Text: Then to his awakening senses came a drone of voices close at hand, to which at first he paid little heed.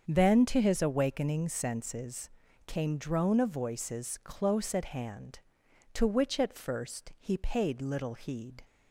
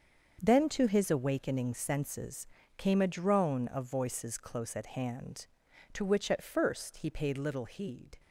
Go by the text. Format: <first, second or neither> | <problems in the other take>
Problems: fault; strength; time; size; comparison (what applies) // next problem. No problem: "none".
second | starts louder than the rest; until 1.0 s; 7 dB; also in the second // pauses between "senses" and "came"; slight; at 2.2 s; 0.36 s long; slight in the second // skips "a"; at 2.9 s